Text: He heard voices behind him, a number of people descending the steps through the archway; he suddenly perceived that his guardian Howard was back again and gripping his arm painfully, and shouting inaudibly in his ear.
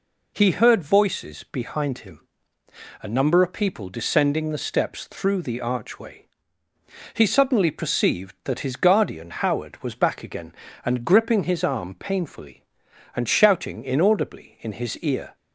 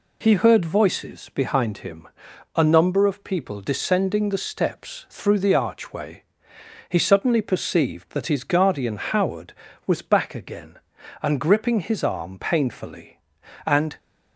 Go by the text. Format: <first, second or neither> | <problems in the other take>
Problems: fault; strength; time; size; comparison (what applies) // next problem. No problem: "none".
first | stops before "shouting inaudibly in his ear"; at 13.9 s